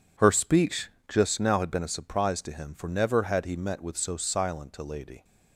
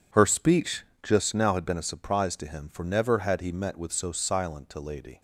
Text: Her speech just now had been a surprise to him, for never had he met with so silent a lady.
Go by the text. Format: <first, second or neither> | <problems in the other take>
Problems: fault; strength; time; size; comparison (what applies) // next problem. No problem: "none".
neither | pauses between "speech" and "just"; slight; the same in both